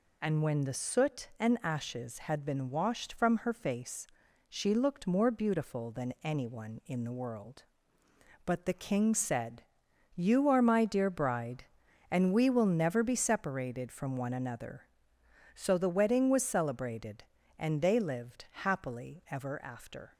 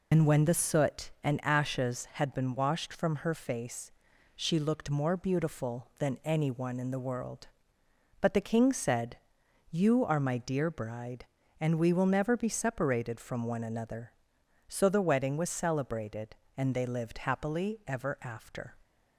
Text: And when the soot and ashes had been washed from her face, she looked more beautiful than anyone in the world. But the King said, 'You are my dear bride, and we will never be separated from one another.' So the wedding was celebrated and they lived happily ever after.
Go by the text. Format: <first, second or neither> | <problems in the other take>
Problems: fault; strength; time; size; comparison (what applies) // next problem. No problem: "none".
first | loses the start of "And"; at 0.1 s; 80 ms